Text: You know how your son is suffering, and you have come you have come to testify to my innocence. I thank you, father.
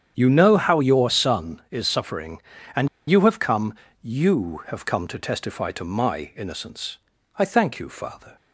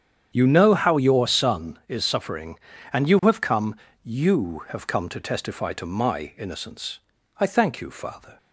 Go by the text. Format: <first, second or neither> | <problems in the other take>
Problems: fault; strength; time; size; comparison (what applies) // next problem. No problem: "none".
second | starts louder than the rest; strong; until 1.1 s; 8 dB; strong in the second // pauses between "and" and "you"; slight; at 2.8 s; 0.19 s long // pauses between "come" and "you"; slight; at 3.7 s; 0.32 s long; slight in the second